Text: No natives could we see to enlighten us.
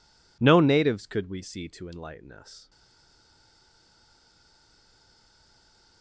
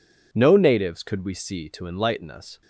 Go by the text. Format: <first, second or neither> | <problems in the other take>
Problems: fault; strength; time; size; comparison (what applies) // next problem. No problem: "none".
second | stays silent after the last word; strong; from 2.6 s on; 3.4 s long